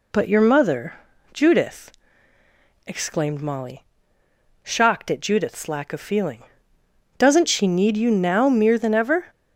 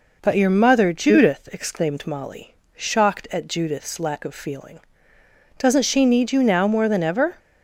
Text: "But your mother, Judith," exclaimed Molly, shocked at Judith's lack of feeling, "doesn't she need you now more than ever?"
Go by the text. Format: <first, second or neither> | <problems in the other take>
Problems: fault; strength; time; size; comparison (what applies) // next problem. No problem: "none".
second | says "mere" for "more"; at 8.4 s